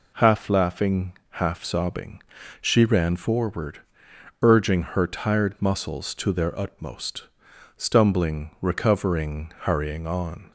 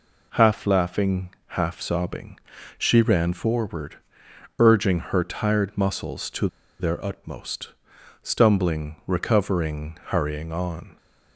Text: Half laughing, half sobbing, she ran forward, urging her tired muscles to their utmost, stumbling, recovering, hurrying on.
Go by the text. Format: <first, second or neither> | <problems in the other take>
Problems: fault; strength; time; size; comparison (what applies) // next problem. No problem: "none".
first | pauses between "to" and "their"; slight; at 6.4 s; 0.32 s long